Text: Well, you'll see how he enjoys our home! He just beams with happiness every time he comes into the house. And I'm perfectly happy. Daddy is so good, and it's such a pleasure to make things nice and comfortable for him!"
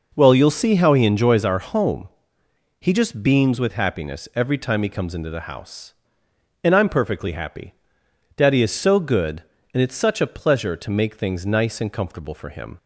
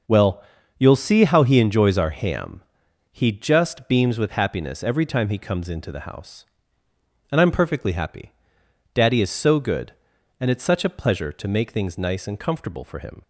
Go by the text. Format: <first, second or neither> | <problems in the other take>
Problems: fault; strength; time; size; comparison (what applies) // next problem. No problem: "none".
first | says "ham" for "home"; at 2.1 s